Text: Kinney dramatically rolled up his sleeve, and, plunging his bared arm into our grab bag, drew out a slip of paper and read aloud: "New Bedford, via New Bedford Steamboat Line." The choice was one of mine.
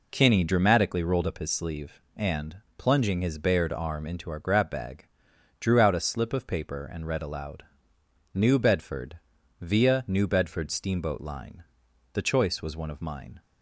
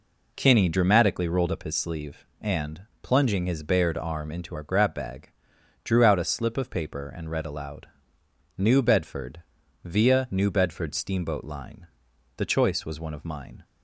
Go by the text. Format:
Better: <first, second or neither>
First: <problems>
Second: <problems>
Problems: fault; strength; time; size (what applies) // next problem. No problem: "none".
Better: neither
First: none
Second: none